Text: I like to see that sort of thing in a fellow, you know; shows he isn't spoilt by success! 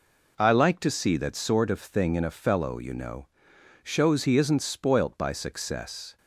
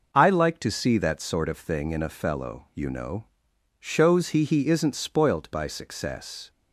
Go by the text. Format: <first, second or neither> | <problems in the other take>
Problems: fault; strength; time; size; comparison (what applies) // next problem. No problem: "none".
first | says "he" twice; at 4.4 s